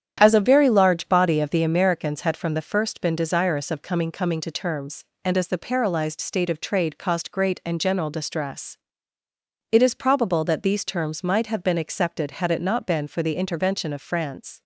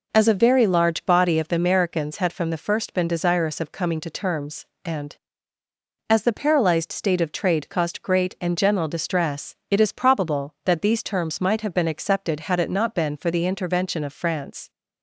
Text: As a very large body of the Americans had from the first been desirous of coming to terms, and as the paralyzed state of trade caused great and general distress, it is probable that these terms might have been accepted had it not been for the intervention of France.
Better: second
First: starts louder than the rest; strong; until 1.2 s; 9 dB // says "coming" twice; at 4.1 s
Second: none

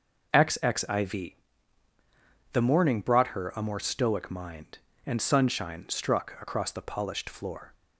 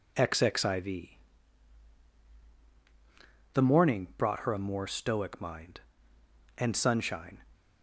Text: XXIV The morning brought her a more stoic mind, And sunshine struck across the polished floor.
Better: first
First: pauses between "XXIV" and "The"; at 1.3 s; 1.2 s long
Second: pauses between "XXIV" and "The"; strong; at 1.1 s; 2.4 s long // stops before "struck across the polished floor"; at 7.5 s

